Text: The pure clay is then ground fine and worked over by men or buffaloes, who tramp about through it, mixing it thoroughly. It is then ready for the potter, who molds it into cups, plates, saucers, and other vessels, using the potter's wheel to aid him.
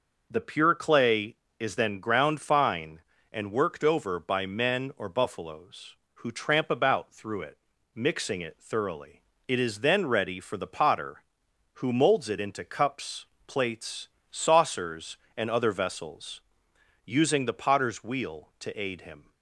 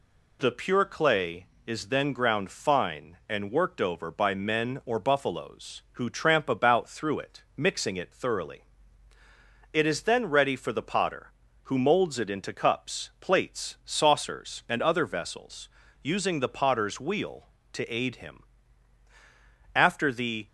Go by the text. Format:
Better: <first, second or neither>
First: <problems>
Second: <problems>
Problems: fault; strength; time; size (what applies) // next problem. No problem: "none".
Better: first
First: none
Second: goes on to say "After the"; noticeable; from 19.7 s on; 0.72 s long